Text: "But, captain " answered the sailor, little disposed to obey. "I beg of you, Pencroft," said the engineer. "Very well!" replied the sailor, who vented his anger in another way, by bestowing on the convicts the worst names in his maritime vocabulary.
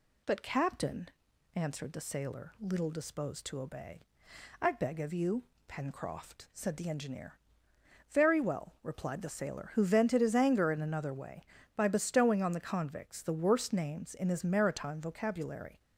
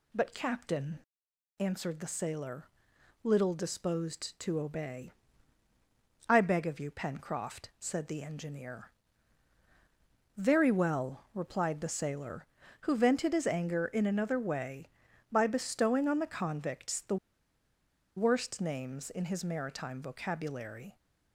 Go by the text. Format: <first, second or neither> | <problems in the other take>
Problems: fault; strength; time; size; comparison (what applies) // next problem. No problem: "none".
first | pauses between "the" and "worst"; at 17.1 s; 1.0 s long